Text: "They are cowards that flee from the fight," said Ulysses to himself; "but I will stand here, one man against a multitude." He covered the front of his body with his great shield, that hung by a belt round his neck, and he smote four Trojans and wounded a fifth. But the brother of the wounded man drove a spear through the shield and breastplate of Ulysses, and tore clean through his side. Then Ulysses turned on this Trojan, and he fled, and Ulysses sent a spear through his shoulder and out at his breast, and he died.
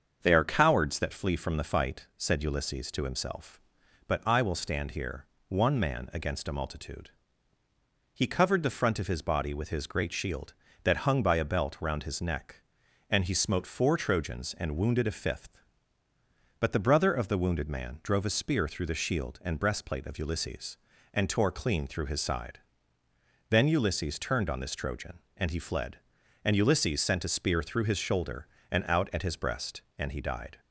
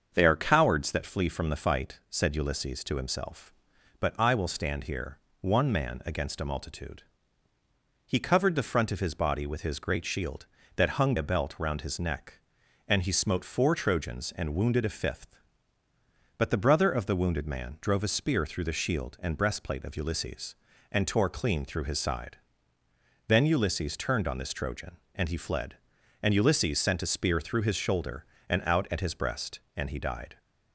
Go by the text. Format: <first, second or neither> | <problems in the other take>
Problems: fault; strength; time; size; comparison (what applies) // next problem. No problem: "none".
first | starts louder than the rest; until 1.1 s; 6.5 dB; also in the first // skips "by"; at 11.1 s